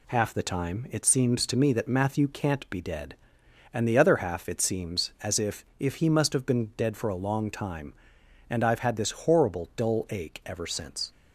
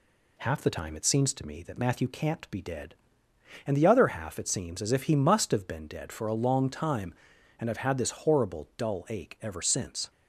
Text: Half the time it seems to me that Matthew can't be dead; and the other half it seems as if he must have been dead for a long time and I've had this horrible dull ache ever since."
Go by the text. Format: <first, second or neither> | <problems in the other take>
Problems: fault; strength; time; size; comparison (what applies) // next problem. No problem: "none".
second | says "if" twice; at 5.7 s